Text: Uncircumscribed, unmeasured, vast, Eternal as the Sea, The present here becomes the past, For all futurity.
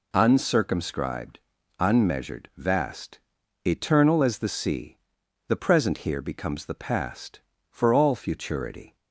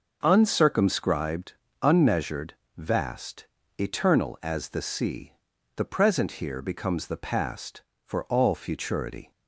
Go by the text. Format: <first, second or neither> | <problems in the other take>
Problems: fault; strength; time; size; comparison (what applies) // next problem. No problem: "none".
neither | none